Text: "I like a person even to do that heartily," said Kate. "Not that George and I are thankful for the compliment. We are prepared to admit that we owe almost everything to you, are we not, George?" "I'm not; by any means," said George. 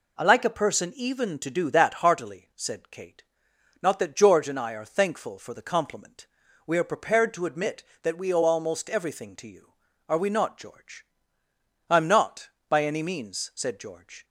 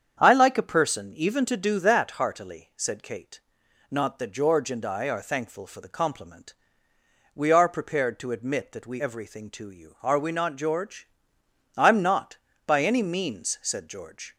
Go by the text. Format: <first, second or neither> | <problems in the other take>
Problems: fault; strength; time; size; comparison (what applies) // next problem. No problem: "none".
first | starts louder than the rest; strong; until 1.2 s; 8 dB // skips "owe almost"; at 9.0 s